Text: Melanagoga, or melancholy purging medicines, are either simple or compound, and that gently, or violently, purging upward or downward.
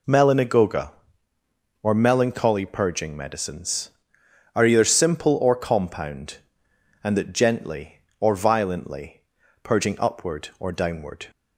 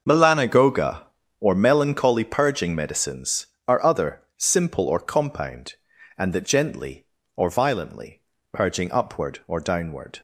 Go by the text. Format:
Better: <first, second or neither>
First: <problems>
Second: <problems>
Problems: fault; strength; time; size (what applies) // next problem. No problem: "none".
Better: first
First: none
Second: says "other" for "either"; at 3.8 s